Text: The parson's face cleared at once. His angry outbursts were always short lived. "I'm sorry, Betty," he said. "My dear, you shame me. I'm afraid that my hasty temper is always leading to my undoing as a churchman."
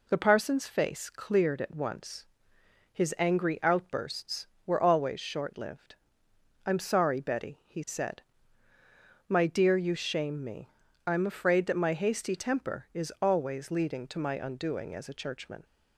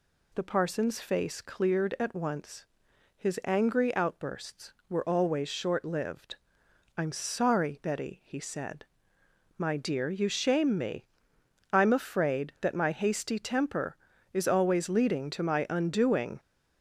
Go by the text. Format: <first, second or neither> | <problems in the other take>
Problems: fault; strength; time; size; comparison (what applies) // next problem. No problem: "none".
first | stops before "as a churchman"; at 16.3 s